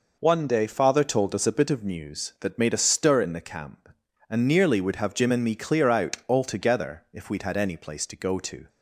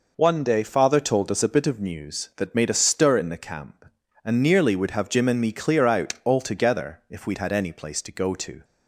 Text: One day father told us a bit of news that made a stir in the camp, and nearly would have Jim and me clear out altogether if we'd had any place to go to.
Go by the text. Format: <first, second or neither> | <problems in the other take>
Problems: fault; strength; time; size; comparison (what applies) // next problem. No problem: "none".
neither | none